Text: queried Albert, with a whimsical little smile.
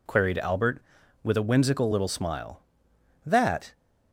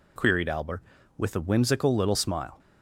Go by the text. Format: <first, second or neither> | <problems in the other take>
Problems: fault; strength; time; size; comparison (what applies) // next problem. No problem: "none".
second | goes on to say "That"; slight; from 3.2 s on; 0.48 s long